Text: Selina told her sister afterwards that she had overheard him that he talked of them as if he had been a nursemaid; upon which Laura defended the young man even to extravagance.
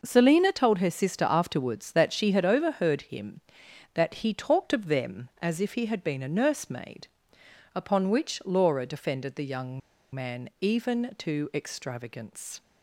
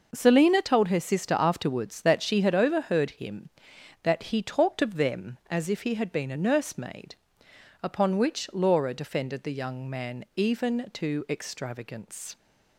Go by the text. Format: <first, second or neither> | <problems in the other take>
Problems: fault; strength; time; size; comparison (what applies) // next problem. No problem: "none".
second | pauses between "young" and "man"; slight; at 9.8 s; 0.33 s long